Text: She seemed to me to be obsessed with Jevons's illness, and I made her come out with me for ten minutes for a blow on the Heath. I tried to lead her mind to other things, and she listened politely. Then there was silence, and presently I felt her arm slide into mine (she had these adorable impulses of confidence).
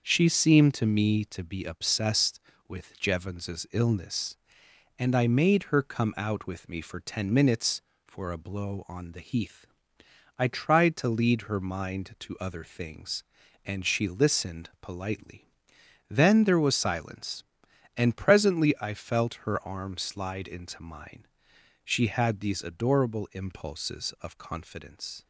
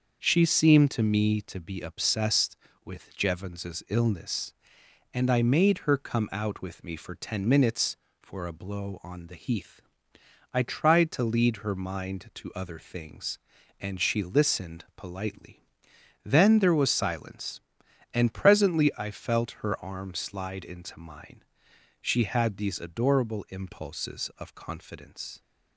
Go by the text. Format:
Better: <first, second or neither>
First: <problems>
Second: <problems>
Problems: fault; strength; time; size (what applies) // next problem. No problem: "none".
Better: neither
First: starts louder than the rest; until 1.0 s; 6.5 dB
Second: starts louder than the rest; until 1.2 s; 6.5 dB